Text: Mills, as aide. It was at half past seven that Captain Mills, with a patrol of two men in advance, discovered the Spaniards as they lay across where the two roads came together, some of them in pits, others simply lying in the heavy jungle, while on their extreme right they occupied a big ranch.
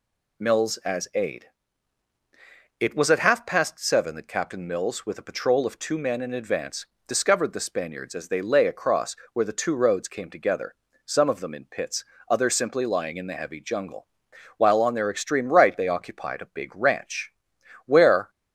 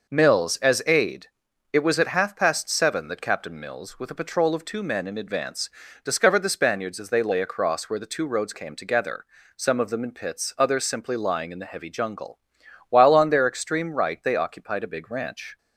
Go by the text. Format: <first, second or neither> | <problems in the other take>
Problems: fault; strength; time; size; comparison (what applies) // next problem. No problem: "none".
second | pauses between "across" and "where"; slight; at 9.1 s; 0.18 s long // goes on to say "Where"; slight; from 17.8 s on; 0.44 s long